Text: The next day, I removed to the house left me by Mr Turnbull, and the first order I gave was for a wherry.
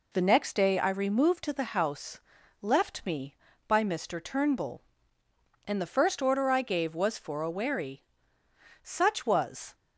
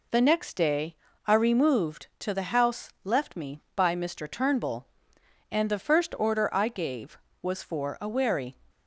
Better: second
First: pauses between "house" and "left"; at 2.1 s; 0.42 s long // goes on to say "Such was"; noticeable; from 8.8 s on; 0.92 s long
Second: none

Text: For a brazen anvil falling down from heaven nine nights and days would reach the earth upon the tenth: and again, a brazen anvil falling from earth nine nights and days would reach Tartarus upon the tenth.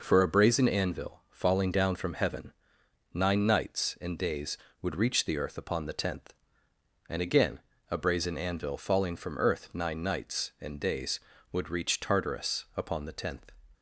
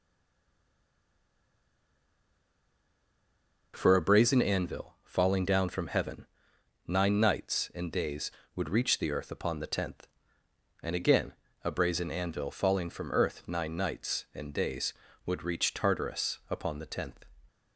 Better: first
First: pauses between "heaven" and "nine"; noticeable; at 2.5 s; 0.60 s long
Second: stays silent before the first word; strong; until 3.7 s; 3.7 s long // pauses between "heaven" and "nine"; noticeable; at 6.2 s; 0.60 s long

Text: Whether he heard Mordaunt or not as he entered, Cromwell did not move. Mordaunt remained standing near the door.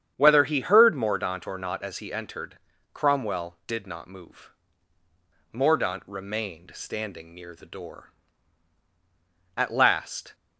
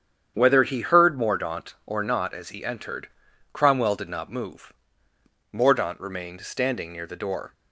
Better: second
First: starts louder than the rest; strong; until 1.1 s; 8.5 dB // goes on to say "At last"; noticeable; from 9.5 s on; 0.78 s long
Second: starts louder than the rest; strong; until 1.3 s; 8.5 dB

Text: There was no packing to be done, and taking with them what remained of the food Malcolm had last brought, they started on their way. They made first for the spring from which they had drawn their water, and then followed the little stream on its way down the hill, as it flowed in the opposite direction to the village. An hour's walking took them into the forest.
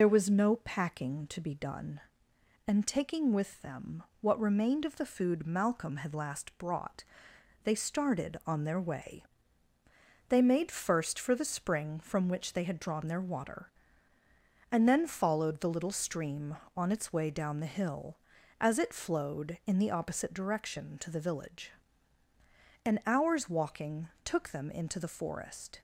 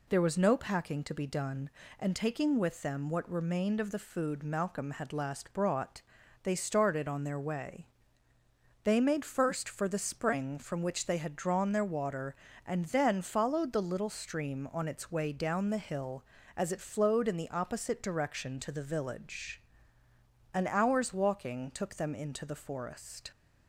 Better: second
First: loses the start of "There"; at 0.0 s; 60 ms // pauses between "them" and "what"; slight; at 4.0 s; 0.16 s long // pauses between "walking" and "took"; slight; at 24.0 s; 0.16 s long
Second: none

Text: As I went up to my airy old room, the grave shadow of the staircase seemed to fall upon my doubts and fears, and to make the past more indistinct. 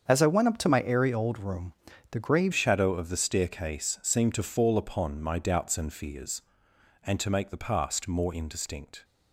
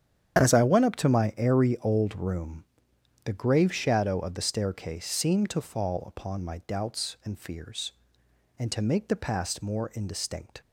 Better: second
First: starts louder than the rest; strong; until 1.1 s; 7 dB // changes voice at "shadow"; from 2.5 s on; 6.5 s long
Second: starts louder than the rest; strong; until 1.4 s; 8.5 dB

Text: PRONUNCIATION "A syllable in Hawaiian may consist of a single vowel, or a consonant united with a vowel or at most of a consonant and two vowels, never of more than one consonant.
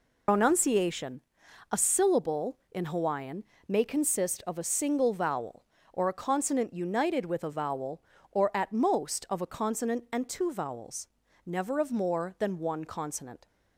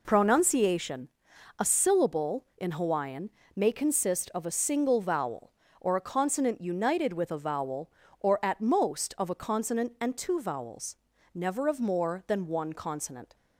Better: second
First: loses the start of "PRONUNCIATION"; at 0.2 s; 105 ms // pauses between "PRONUNCIATION" and "A"; noticeable; at 1.2 s; 0.50 s long // pauses between "Hawaiian" and "may"; slight; at 3.4 s; 0.22 s long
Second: pauses between "PRONUNCIATION" and "A"; noticeable; at 1.0 s; 0.50 s long // pauses between "Hawaiian" and "may"; slight; at 3.3 s; 0.24 s long

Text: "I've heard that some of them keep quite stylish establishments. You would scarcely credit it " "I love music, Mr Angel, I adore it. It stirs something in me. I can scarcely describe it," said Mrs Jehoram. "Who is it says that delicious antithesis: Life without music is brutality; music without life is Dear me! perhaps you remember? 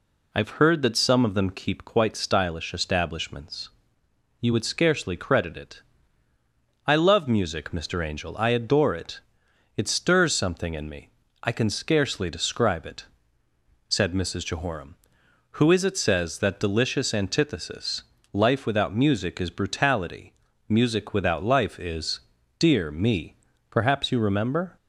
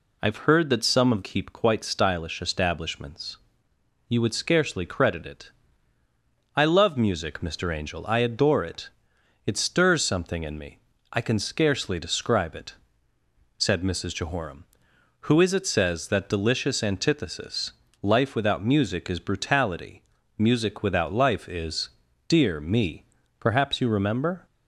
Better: first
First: pauses between "is" and "Dear"; at 22.2 s; 0.38 s long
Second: skips "them"; at 1.2 s // pauses between "is" and "Dear"; at 21.8 s; 0.38 s long

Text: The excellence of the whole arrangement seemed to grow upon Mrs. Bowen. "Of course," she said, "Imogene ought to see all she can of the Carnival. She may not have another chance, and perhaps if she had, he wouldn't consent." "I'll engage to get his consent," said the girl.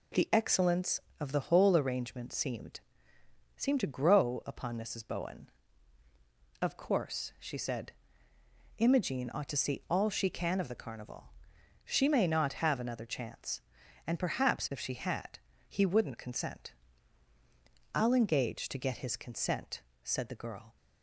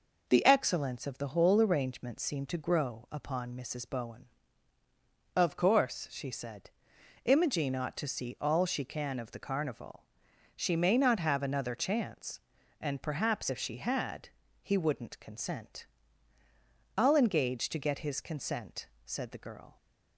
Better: second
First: says "seemed" twice; at 3.5 s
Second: none

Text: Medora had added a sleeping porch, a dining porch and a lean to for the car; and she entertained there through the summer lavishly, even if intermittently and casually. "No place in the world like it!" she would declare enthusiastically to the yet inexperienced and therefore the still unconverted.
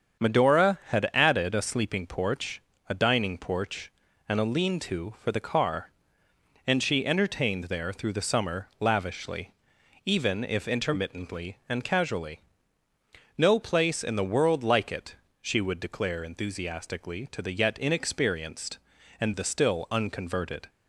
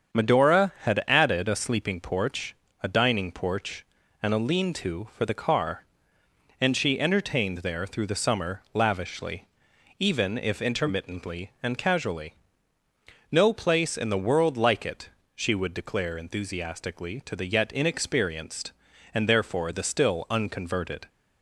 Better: second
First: starts louder than the rest; strong; until 1.3 s; 7.5 dB // skips "therefore"; at 19.3 s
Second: starts louder than the rest; strong; until 1.2 s; 7.5 dB

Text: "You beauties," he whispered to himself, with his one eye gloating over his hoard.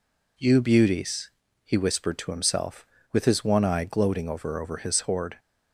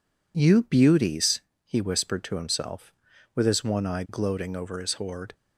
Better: second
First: says "over" twice; at 4.5 s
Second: none

